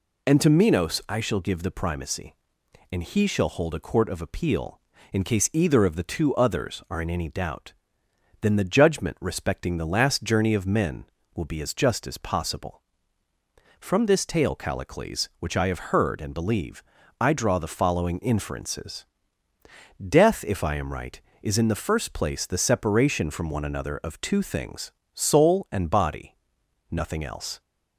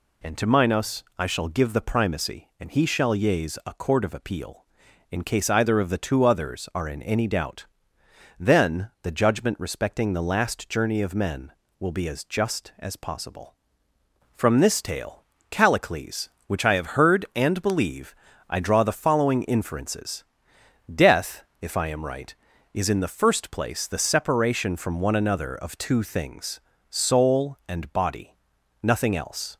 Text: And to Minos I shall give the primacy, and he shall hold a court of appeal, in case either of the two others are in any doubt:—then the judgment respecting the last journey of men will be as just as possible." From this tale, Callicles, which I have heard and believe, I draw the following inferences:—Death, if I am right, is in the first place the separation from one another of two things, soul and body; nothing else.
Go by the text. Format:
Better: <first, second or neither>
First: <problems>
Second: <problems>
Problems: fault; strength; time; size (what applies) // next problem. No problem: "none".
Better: first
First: none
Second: says "yeas" for "hold"; at 3.1 s